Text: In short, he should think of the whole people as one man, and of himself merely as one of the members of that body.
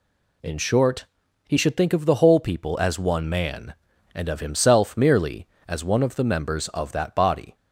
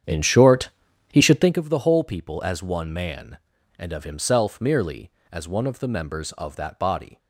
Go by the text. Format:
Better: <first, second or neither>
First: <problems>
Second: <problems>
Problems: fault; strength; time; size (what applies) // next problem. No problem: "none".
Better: first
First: none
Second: starts louder than the rest; strong; until 1.6 s; 9 dB